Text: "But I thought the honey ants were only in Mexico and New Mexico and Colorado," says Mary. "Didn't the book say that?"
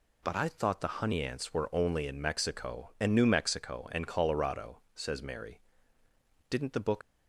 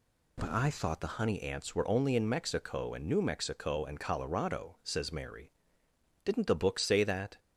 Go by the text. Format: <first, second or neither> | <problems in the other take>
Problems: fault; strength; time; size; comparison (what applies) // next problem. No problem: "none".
second | stops before "say that"; at 7.0 s